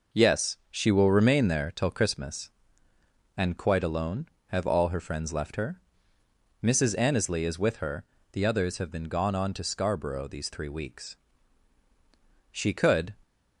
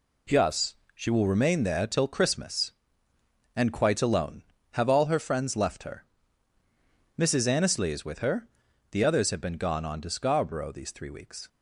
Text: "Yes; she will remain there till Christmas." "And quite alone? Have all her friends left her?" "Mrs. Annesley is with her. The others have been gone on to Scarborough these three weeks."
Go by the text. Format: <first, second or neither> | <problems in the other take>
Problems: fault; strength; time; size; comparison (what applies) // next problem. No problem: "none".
second | goes on to say "She could"; noticeable; from 12.5 s on; 0.62 s long